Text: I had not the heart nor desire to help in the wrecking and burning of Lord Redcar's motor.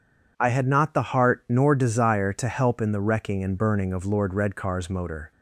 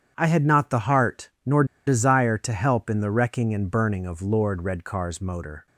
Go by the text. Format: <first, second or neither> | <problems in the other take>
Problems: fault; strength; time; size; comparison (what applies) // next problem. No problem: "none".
first | starts louder than the rest; strong; until 1.1 s; 8.5 dB // pauses between "nor" and "desire"; slight; at 1.6 s; 0.22 s long